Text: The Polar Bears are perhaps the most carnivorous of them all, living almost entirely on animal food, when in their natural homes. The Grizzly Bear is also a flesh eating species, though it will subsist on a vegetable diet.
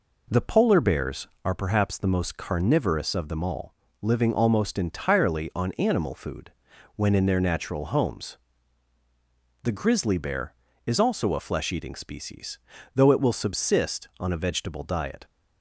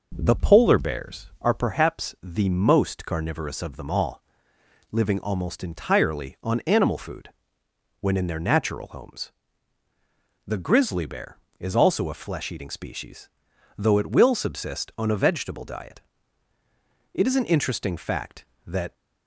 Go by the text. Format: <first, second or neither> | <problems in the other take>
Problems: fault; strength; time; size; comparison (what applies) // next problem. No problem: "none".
first | goes on to say "It is an interesting fact that"; strong; from 17.1 s on; 1.7 s long